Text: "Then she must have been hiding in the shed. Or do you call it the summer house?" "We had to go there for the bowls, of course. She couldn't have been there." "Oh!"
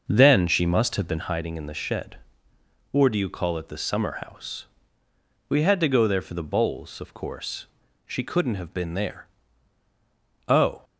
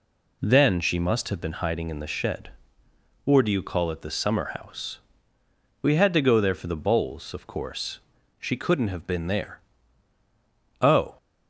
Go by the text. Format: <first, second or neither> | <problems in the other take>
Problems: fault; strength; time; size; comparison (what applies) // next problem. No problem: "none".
second | starts louder than the rest; noticeable; until 1.3 s; 6 dB